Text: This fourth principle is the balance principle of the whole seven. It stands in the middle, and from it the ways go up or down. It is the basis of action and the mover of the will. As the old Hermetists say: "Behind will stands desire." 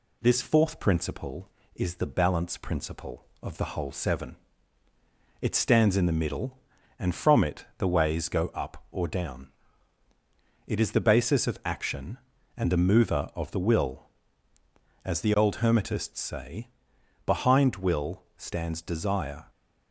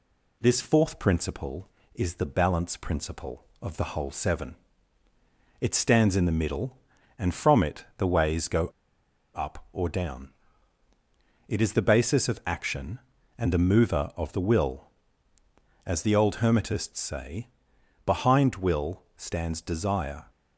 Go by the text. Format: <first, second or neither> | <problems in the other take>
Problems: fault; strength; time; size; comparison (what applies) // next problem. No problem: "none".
first | pauses between "go" and "up"; noticeable; at 8.6 s; 0.67 s long